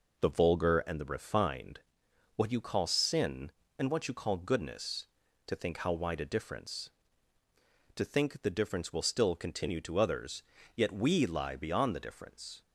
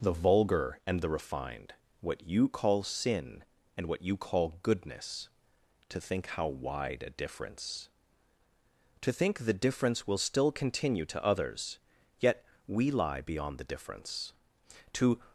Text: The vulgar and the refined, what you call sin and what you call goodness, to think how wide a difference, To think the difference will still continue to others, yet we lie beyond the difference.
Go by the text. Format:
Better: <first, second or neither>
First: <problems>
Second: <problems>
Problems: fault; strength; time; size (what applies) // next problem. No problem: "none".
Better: first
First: none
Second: pauses between "yet" and "we"; slight; at 12.4 s; 0.24 s long // goes on to say "To"; slight; from 14.9 s on; 0.28 s long